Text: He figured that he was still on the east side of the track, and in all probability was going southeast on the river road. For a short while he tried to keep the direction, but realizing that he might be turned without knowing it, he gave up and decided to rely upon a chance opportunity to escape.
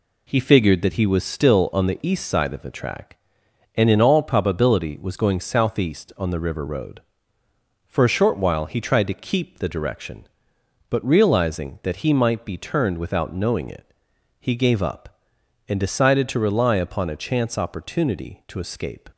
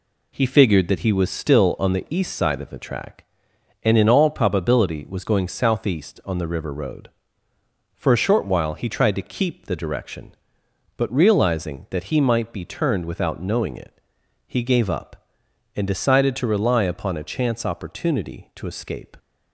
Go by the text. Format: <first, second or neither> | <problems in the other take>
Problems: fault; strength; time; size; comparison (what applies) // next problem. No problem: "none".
neither | none